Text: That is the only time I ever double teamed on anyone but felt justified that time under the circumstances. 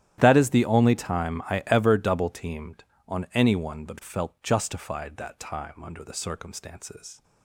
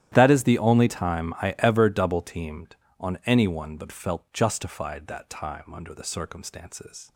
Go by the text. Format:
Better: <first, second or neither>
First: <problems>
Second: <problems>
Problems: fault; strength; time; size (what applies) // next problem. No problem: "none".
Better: neither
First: starts louder than the rest; strong; until 1.1 s; 12 dB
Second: starts louder than the rest; strong; until 1.1 s; 12 dB